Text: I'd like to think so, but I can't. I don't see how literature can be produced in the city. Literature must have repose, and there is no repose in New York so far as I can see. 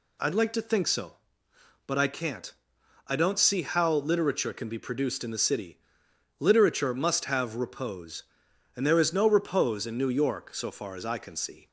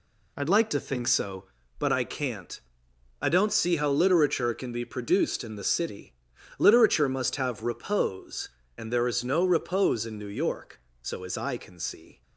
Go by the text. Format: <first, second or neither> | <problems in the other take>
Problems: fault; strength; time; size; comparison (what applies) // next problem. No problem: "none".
first | skips "far"; at 11.2 s